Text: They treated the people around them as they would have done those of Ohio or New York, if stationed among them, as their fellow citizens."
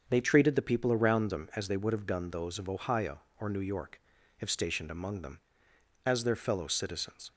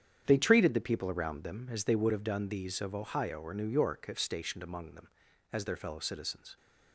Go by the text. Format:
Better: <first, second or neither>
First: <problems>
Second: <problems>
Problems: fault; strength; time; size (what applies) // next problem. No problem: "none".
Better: first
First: starts louder than the rest; until 1.0 s; 7 dB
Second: starts louder than the rest; strong; until 1.2 s; 9 dB // says "these" for "those"; at 2.4 s